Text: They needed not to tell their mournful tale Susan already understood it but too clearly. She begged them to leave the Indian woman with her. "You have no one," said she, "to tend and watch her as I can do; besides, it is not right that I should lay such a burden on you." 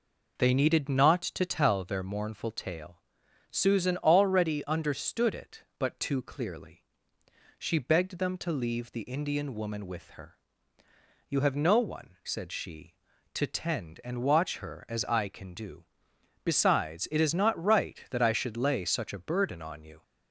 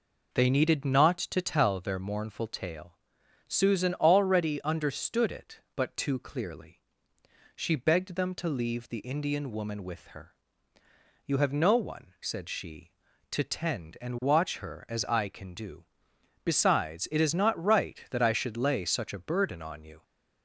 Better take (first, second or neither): neither